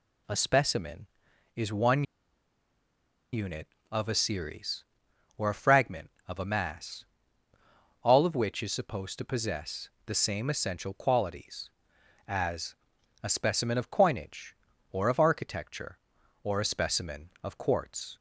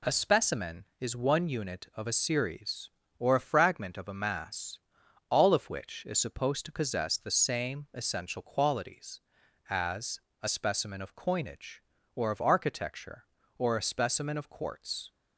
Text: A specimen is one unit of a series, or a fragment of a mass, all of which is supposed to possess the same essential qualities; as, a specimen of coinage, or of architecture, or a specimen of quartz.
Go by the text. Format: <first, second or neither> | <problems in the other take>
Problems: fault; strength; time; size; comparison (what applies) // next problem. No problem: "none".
second | pauses between "one" and "unit"; strong; at 2.0 s; 1.3 s long // pauses between "possess" and "the"; slight; at 9.9 s; 0.16 s long